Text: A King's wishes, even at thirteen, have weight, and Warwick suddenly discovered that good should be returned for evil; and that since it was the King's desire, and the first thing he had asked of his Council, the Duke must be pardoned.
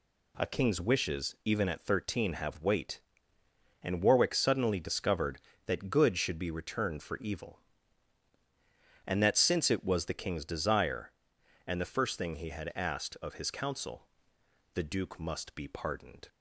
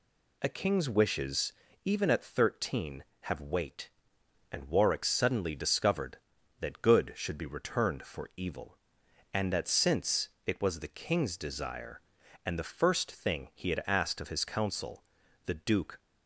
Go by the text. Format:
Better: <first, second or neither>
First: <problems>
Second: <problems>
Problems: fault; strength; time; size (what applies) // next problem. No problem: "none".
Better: first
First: none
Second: pauses between "since" and "it"; slight; at 10.2 s; 0.16 s long // stops before "must be pardoned"; at 15.9 s